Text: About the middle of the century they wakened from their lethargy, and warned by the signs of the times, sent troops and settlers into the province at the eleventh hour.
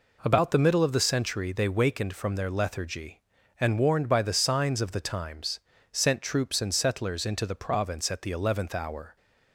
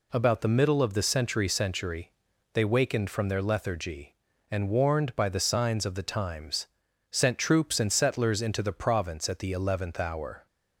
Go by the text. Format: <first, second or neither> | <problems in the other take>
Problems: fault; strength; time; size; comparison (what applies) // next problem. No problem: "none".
first | says "century" twice; at 1.4 s